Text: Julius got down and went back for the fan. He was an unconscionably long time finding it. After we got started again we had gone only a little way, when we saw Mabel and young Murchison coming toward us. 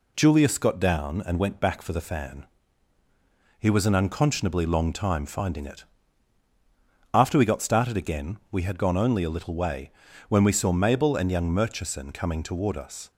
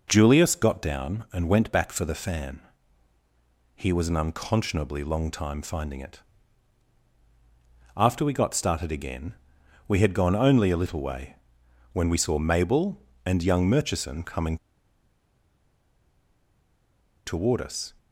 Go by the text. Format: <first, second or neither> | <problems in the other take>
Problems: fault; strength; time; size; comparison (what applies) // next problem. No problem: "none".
first | pauses between "again" and "we"; noticeable; at 9.3 s; 0.52 s long // pauses between "coming" and "toward"; strong; at 14.5 s; 2.6 s long